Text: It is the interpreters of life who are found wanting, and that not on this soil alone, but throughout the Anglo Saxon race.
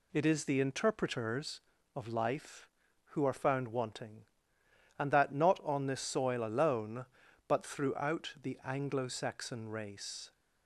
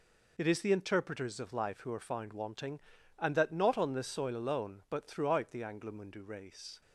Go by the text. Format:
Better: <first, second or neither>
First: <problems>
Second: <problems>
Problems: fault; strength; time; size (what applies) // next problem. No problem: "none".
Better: first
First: none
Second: says "Mundu" for "Saxon"; at 5.9 s